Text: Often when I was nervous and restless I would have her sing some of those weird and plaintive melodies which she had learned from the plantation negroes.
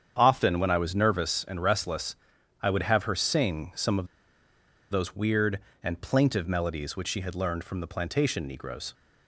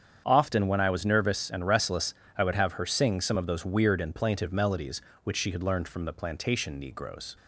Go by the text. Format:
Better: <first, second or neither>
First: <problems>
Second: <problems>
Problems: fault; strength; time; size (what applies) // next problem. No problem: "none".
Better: second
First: starts louder than the rest; strong; until 1.1 s; 8 dB // pauses between "restless" and "I"; noticeable; at 2.1 s; 0.48 s long // pauses between "of" and "those"; noticeable; at 4.0 s; 0.84 s long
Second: starts louder than the rest; strong; until 1.2 s; 8 dB // pauses between "restless" and "I"; slight; at 2.1 s; 0.24 s long